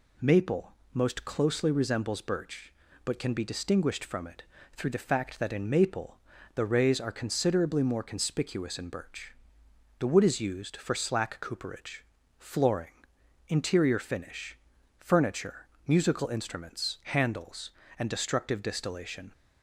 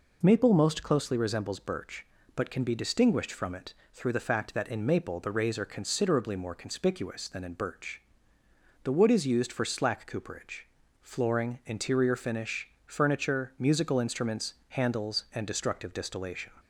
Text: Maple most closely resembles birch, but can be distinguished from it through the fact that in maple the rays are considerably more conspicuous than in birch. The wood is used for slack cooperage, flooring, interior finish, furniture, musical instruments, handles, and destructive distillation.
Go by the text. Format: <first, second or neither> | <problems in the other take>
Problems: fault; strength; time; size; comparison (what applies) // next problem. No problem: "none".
second | pauses between "Maple" and "most"; slight; at 0.7 s; 0.22 s long // pauses between "it" and "through"; slight; at 4.4 s; 0.28 s long; slight in the second // pauses between "maple" and "the"; at 6.1 s; 0.38 s long // skips "than"; at 8.7 s